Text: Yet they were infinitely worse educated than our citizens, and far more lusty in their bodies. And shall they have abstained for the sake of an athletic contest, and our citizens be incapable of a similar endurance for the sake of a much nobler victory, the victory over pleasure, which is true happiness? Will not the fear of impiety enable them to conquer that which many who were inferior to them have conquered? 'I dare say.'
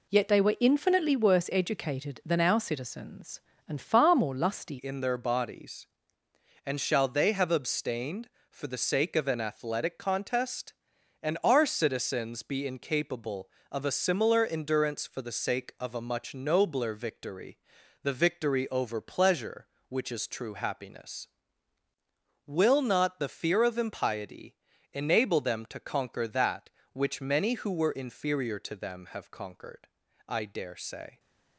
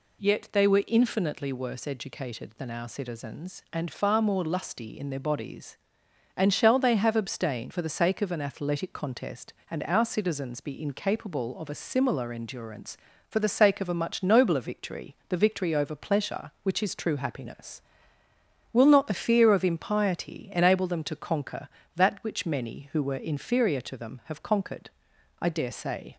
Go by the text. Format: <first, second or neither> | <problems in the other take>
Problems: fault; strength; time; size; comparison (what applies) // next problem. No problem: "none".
second | changes voice at "in"; from 4.7 s on; 26.4 s long // pauses between "impiety" and "enable"; slight; at 24.5 s; 0.36 s long